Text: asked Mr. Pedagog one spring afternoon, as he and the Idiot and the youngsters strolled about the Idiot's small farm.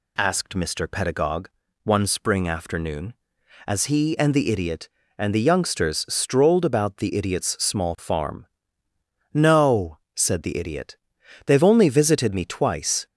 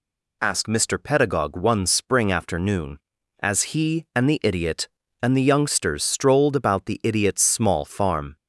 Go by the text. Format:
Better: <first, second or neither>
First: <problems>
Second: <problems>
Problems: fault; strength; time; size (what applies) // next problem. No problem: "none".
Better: second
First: pauses between "Pedagog" and "one"; slight; at 1.4 s; 0.34 s long // goes on to say "No said the Idiot They've only visited me twice"; strong; from 9.3 s on; 3.7 s long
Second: none